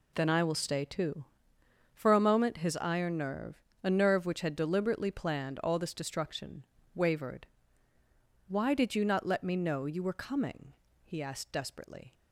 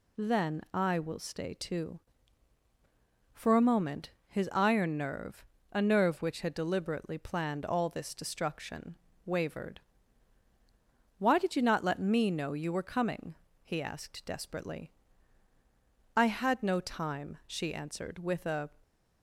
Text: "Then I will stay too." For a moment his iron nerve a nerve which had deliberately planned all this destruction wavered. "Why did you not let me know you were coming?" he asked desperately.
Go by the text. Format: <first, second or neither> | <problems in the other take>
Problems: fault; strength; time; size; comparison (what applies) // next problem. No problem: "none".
first | pauses between "moment" and "his"; slight; at 4.1 s; 0.16 s long // pauses between "nerve" and "a"; slight; at 5.4 s; 0.28 s long; slight in the first // pauses between "destruction" and "wavered"; slight; at 8.9 s; 0.30 s long; slight in the first // goes on to say "I had no time she answered with a"; strong; from 16.1 s on; 2.5 s long